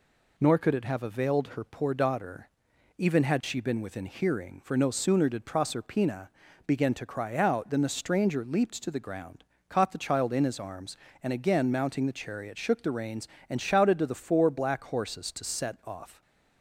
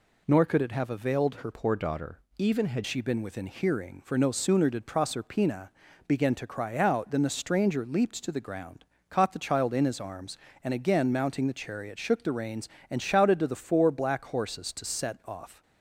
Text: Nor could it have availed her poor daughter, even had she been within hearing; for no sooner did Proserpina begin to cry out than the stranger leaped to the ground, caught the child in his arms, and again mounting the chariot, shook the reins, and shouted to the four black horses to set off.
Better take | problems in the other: first | changes voice from "poor" to "had"; from 1.5 to 2.8 s; 1.3 s long // pauses between "Proserpina" and "begin"; slight; at 5.6 s; 0.36 s long; slight in the first

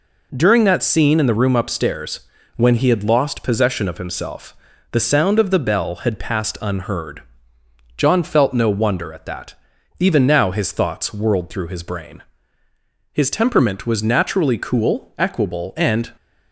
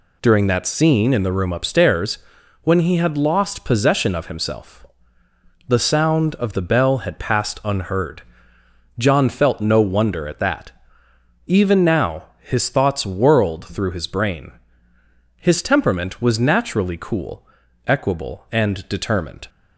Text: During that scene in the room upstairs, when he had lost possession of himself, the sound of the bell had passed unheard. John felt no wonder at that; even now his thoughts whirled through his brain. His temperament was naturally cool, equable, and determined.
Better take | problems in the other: second | stops before "determined"; at 16.1 s

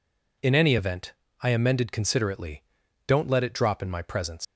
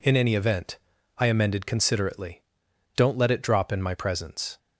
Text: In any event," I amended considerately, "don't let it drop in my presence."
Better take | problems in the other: second | leaves "presence" unfinished; at 4.4 s; 125 ms

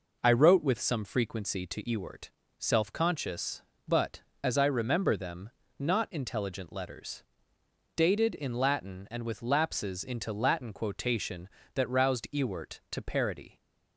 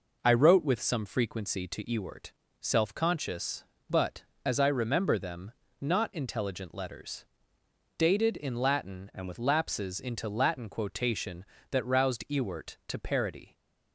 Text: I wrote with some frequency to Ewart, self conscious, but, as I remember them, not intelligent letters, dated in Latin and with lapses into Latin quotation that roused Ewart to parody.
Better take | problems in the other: first | changes voice from "and" to "with"; from 9.1 to 9.3 s; 0.2 s long

